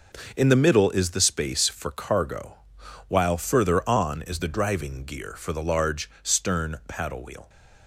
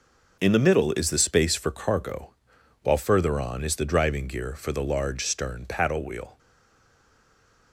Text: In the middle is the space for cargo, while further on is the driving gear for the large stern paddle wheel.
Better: first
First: none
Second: stays silent after the last word; noticeable; from 6.3 s on; 1.4 s long

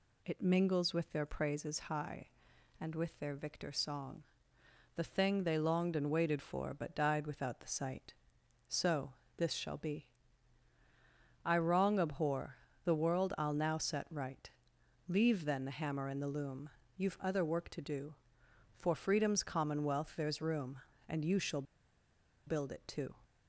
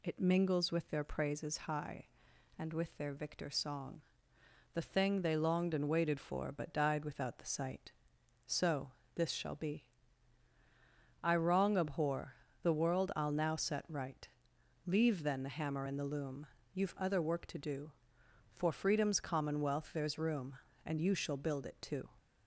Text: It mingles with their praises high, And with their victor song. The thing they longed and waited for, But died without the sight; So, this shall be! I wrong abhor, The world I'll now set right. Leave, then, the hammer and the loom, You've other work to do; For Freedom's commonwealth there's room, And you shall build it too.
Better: second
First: pauses between "shall" and "build"; noticeable; at 21.6 s; 0.84 s long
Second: none

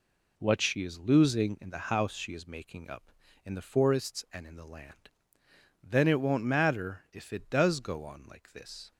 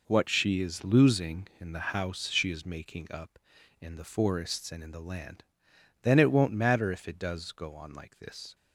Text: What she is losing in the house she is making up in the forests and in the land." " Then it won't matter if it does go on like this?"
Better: first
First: none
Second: gets quieter; strong; throughout; 10 dB

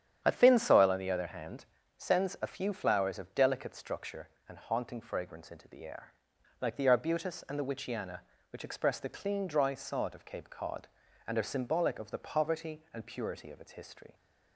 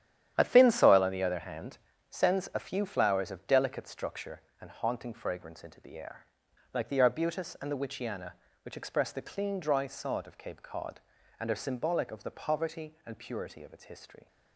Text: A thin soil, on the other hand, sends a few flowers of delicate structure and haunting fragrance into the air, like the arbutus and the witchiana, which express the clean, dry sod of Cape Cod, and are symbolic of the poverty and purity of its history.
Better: first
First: starts louder than the rest; strong; until 1.2 s; 9 dB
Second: gets quieter; strong; throughout; 10 dB // starts louder than the rest; strong; until 1.3 s; 10.5 dB

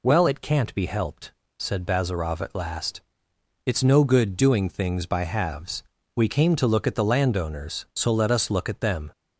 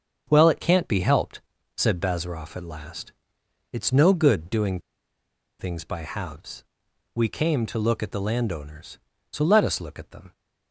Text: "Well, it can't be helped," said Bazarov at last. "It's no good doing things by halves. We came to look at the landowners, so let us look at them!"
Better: first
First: none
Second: starts louder than the rest; until 1.3 s; 7 dB // pauses between "doing" and "things"; noticeable; at 4.7 s; 0.80 s long

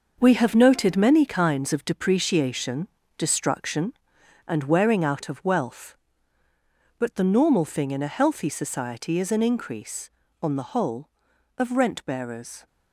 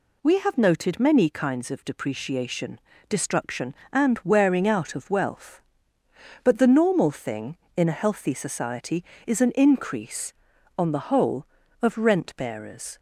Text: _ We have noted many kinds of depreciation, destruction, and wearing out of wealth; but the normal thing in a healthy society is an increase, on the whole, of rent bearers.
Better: second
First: gets quieter; strong; throughout; 9.5 dB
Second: none

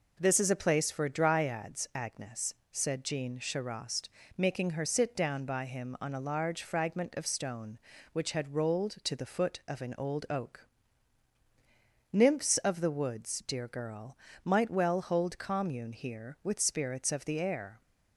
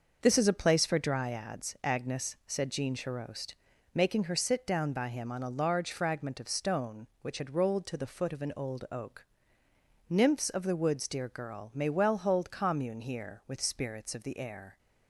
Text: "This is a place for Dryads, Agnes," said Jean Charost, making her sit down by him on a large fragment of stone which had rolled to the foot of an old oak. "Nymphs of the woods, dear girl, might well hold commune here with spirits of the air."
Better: first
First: none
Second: starts louder than the rest; noticeable; until 1.2 s; 6 dB // says "may" for "might"; at 11.7 s

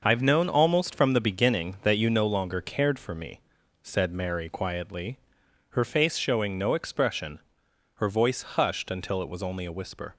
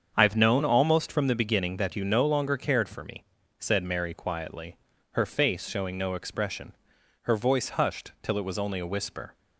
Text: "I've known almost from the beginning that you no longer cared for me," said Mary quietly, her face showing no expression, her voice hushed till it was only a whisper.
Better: second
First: starts louder than the rest; noticeable; until 1.0 s; 6 dB // says "until" for "till"; at 8.9 s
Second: starts louder than the rest; strong; until 1.1 s; 7.5 dB

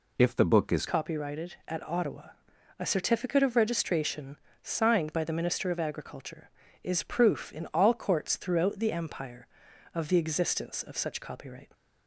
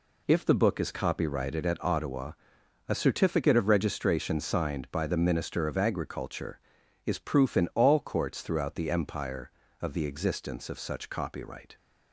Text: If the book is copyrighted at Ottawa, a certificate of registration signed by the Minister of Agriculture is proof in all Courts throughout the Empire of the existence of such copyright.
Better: second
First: changes voice at "copyrighted"; from 0.8 s on; 10.9 s long // pauses between "registration" and "signed"; slight; at 4.3 s; 0.24 s long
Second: none

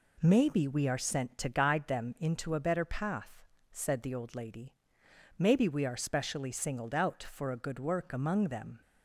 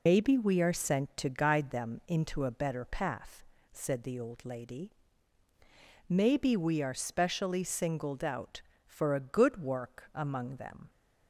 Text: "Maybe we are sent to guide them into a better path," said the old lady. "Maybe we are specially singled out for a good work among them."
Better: first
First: none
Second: loses the start of "Maybe"; at 0.0 s; 115 ms

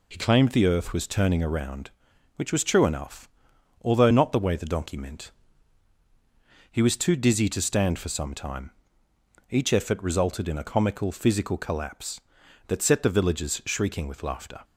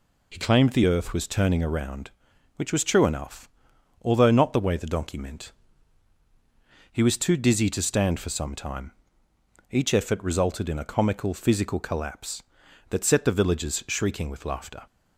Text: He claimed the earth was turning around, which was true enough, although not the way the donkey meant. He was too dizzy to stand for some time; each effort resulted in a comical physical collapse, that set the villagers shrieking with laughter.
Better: neither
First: none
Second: none

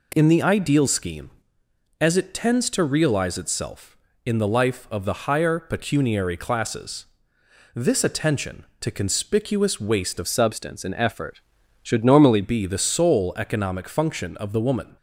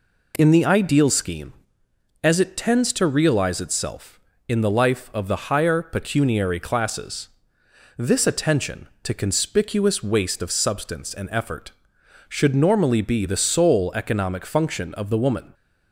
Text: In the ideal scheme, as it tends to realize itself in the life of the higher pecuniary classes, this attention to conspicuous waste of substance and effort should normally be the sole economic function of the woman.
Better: second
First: changes voice from "substance" to "normally"; from 10.2 to 12.4 s; 2.2 s long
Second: none

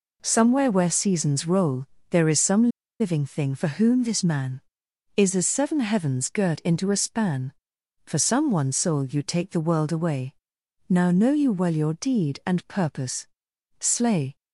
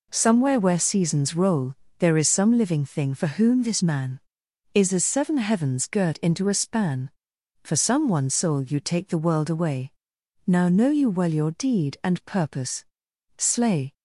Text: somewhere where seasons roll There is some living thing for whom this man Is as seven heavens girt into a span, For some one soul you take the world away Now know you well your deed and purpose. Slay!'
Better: second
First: pauses between "roll" and "There"; slight; at 1.8 s; 0.24 s long // pauses between "some" and "living"; slight; at 2.6 s; 0.32 s long // pauses between "away" and "Now"; noticeable; at 10.3 s; 0.56 s long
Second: pauses between "roll" and "There"; slight; at 1.7 s; 0.24 s long // pauses between "away" and "Now"; noticeable; at 9.9 s; 0.56 s long

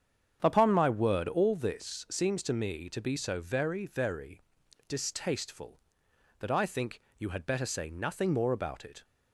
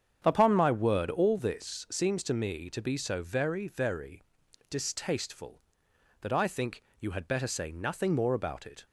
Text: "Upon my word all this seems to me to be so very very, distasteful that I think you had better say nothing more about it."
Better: neither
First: starts louder than the rest; strong; until 1.4 s; 8 dB // pauses between "think" and "you"; slight; at 7.0 s; 0.16 s long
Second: starts louder than the rest; strong; until 1.2 s; 8 dB // pauses between "think" and "you"; slight; at 6.8 s; 0.16 s long

